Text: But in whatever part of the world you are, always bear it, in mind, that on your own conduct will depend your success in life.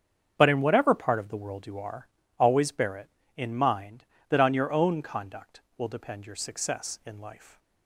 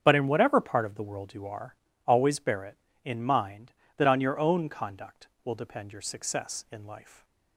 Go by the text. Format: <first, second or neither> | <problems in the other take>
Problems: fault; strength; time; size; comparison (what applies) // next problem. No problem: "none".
neither | starts louder than the rest; strong; the same in both